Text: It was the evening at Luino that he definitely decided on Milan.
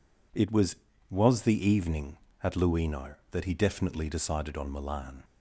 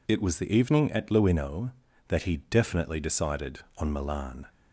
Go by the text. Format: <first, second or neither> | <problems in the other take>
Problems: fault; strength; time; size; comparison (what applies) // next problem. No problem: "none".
second | says "was" twice; at 1.0 s